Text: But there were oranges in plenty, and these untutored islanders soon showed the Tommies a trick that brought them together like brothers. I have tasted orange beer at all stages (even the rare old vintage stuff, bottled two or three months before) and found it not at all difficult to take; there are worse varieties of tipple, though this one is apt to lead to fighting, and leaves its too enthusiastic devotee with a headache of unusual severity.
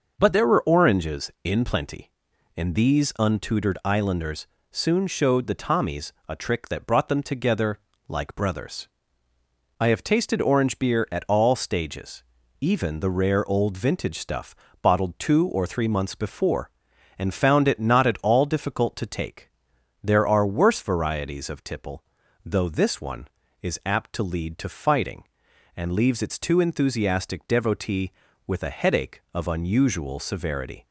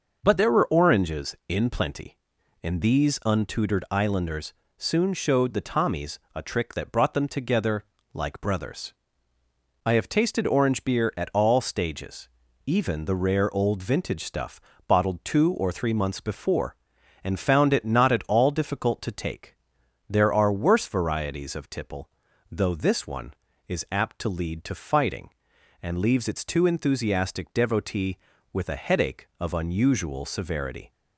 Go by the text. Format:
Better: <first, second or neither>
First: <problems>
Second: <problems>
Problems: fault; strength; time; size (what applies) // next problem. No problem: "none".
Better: neither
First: pauses between "islanders" and "soon"; slight; at 4.4 s; 0.24 s long // pauses between "Tommies" and "a"; slight; at 6.1 s; 0.16 s long // pauses between "together" and "like"; slight; at 7.7 s; 0.30 s long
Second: pauses between "islanders" and "soon"; slight; at 4.5 s; 0.24 s long // pauses between "Tommies" and "a"; slight; at 6.1 s; 0.16 s long // pauses between "together" and "like"; slight; at 7.8 s; 0.30 s long